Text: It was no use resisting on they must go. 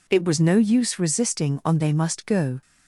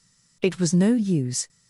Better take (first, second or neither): first